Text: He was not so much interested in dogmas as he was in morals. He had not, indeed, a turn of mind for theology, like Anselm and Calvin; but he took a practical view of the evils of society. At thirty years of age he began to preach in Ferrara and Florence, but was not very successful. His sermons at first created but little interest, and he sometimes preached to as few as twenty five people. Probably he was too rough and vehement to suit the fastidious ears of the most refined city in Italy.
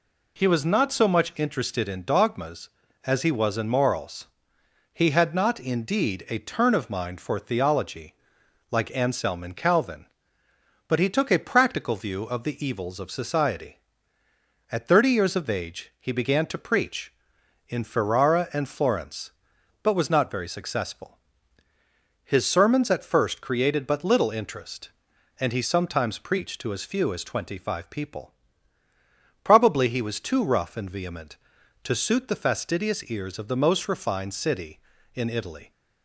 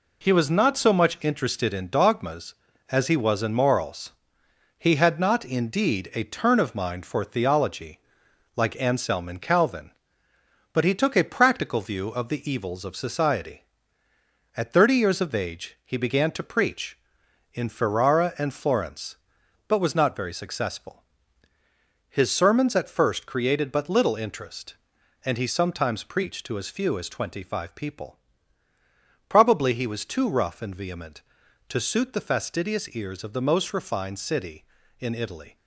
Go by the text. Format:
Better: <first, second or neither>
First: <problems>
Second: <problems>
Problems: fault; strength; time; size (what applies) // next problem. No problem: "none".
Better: first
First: none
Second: gets quieter; throughout; 6.5 dB